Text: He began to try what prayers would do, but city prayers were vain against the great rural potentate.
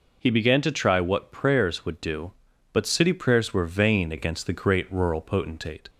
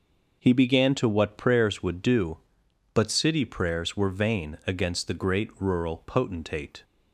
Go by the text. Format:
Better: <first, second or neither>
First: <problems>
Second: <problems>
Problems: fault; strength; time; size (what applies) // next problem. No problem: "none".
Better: first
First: none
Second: skips "try"; at 1.0 s